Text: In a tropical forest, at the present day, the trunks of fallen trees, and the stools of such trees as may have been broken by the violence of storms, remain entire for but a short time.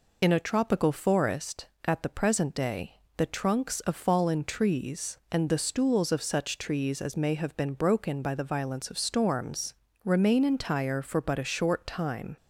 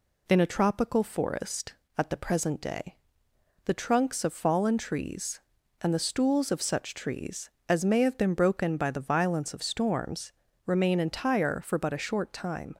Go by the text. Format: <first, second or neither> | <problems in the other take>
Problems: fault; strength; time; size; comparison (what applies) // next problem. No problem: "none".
second | loses the start of "In"; at 0.2 s; 30 ms